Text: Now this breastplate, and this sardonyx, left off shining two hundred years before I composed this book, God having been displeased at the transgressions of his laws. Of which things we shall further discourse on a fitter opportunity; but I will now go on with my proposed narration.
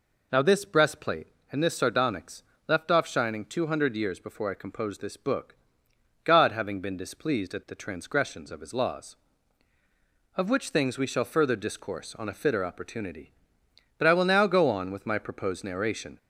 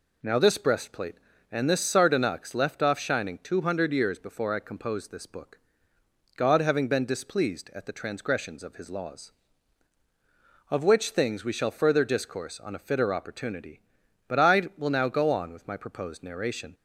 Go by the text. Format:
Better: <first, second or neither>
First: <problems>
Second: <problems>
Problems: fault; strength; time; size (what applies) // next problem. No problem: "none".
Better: neither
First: none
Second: none